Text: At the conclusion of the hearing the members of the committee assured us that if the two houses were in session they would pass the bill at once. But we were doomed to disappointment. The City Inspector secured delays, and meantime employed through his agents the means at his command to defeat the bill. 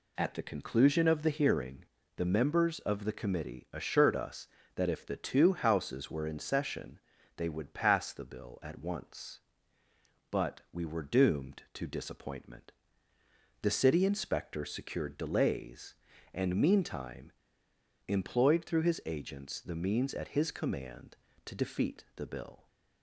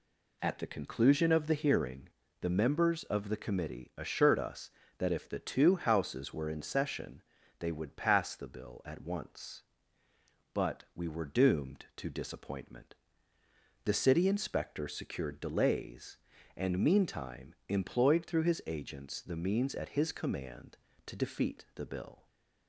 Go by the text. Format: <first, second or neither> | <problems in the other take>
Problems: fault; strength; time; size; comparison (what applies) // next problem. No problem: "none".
second | pauses between "hearing" and "the"; slight; at 1.8 s; 0.32 s long; slight in the second // pauses between "session" and "they"; slight; at 6.9 s; 0.36 s long; slight in the second // pauses between "meantime" and "employed"; noticeable; at 17.3 s; 0.72 s long